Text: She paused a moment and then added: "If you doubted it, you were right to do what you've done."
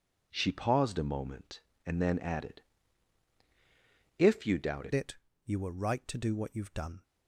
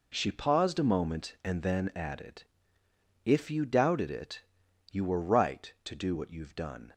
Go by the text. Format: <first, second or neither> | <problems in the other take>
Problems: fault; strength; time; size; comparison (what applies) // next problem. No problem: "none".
second | changes voice at "it"; from 4.9 s on; 2.1 s long